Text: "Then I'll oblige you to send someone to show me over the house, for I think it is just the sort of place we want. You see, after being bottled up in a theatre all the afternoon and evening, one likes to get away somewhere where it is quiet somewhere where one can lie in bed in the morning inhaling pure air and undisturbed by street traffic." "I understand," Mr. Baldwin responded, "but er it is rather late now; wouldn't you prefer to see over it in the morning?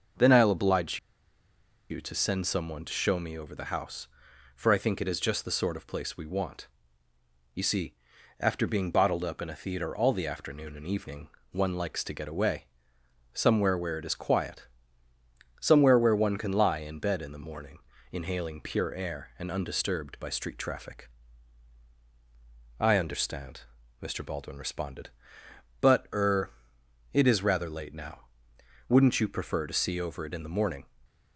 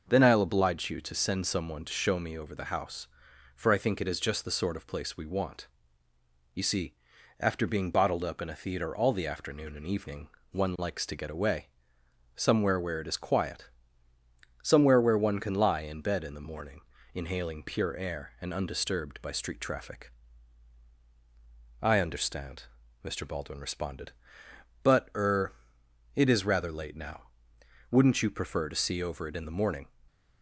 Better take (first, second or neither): second